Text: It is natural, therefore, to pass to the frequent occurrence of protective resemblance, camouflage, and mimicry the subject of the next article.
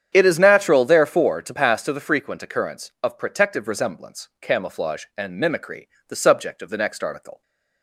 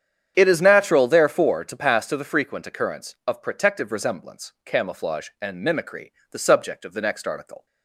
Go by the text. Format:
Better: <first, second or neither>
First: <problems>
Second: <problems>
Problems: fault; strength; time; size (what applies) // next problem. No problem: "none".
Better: neither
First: starts louder than the rest; strong; until 1.1 s; 8.5 dB // pauses between "mimicry" and "the"; slight; at 5.8 s; 0.22 s long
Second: starts louder than the rest; strong; until 1.3 s; 8.5 dB // pauses between "mimicry" and "the"; slight; at 6.1 s; 0.20 s long